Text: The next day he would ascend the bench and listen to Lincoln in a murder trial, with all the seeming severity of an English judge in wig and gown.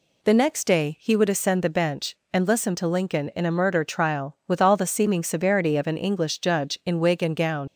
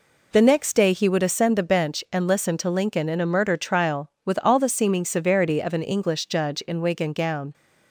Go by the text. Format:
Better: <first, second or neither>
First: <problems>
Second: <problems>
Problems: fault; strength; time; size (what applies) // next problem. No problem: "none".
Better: second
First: leaves "gown" unfinished; at 7.6 s; 75 ms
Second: none